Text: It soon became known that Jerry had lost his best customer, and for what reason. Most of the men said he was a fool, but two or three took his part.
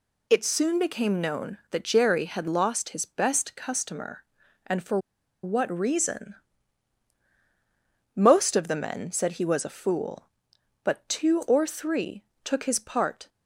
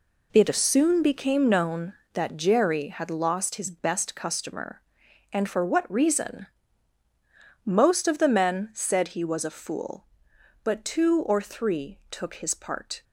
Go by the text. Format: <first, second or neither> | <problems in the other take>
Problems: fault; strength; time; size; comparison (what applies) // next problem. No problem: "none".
second | pauses between "for" and "what"; at 4.9 s; 0.45 s long // pauses between "three" and "took"; slight; at 12.2 s; 0.22 s long